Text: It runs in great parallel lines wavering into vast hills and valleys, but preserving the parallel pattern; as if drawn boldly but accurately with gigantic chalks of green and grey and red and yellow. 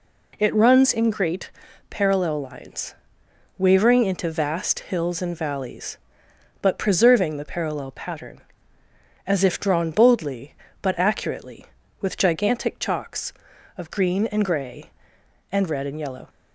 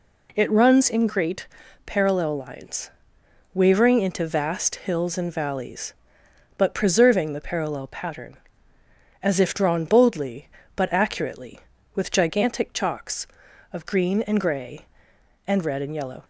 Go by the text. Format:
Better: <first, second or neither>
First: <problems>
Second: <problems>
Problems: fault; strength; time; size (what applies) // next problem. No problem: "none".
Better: neither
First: pauses between "great" and "parallel"; at 1.5 s; 0.40 s long // pauses between "lines" and "wavering"; noticeable; at 2.9 s; 0.62 s long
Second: pauses between "great" and "parallel"; at 1.4 s; 0.39 s long // pauses between "lines" and "wavering"; noticeable; at 2.9 s; 0.62 s long